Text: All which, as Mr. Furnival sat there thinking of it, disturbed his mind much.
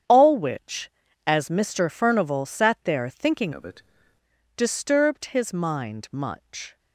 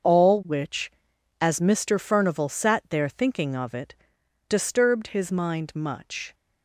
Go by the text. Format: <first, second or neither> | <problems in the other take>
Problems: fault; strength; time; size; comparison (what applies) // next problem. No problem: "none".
second | starts louder than the rest; strong; until 1.4 s; 9 dB; also in the second // changes voice from "of" to "it"; from 3.5 to 3.8 s; 0.3 s long